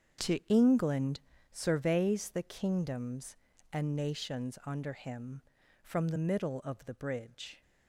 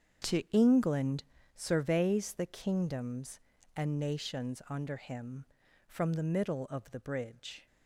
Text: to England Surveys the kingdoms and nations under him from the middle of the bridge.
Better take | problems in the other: neither | starts louder than the rest; strong; the same in both // pauses between "England" and "Surveys"; slight; the same in both

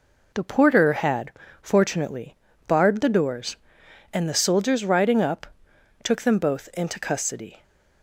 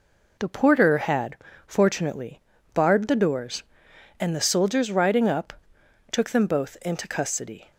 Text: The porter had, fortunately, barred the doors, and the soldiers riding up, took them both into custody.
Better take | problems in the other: neither | none

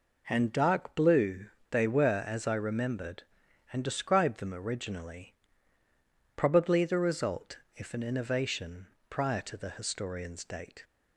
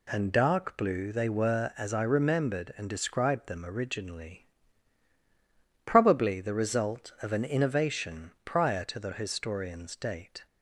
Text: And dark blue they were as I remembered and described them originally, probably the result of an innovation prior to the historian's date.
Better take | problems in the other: second | pauses between "blue" and "they"; slight; at 1.4 s; 0.23 s long // says "if" for "of"; at 7.7 s // pauses between "innovation" and "prior"; slight; at 8.8 s; 0.20 s long

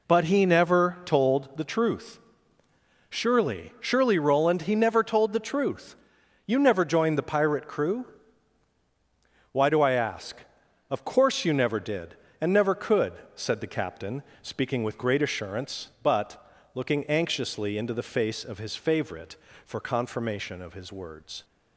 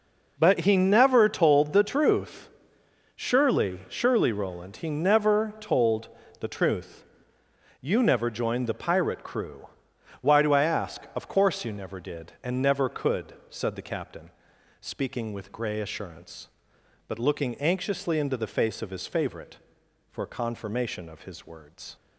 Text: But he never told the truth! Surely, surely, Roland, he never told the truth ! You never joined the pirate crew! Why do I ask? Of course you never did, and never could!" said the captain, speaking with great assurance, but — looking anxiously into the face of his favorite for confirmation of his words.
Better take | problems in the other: first | pauses between "told" and "the"; slight; at 6.0 s; 0.32 s long // says "grey" for "great"; at 15.5 s

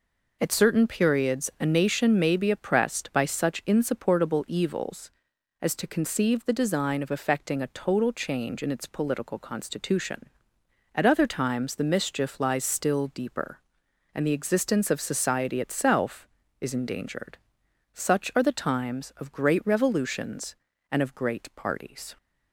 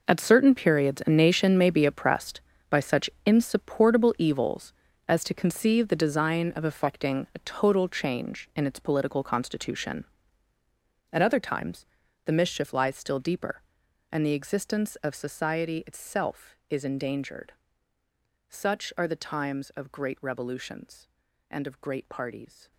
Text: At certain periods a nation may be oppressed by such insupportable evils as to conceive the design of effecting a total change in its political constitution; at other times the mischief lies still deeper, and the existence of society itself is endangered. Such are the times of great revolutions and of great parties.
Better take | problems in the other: first | gets quieter; strong; throughout; 14 dB // pauses between "such" and "insupportable"; slight; at 3.0 s; 0.16 s long // pauses between "times" and "the"; at 11.8 s; 0.40 s long

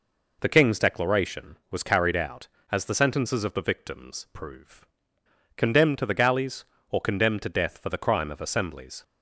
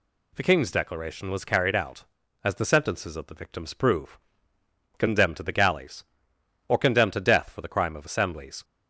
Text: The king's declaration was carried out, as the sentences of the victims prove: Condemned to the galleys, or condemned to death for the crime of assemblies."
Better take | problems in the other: neither | none

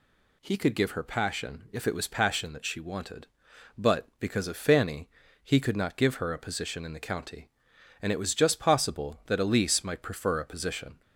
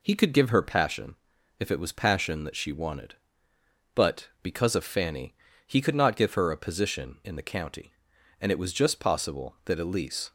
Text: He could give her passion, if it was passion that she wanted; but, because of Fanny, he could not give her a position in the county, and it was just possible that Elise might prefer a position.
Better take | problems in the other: first | stops before "might prefer a position"; at 10.2 s

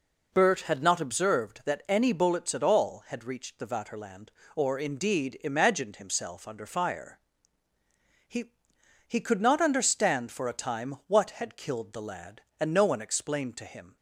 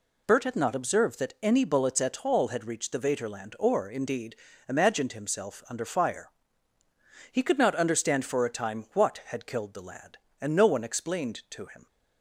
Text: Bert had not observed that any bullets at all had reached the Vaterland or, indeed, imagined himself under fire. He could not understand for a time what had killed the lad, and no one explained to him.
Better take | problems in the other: second | says "He" twice; at 9.0 s

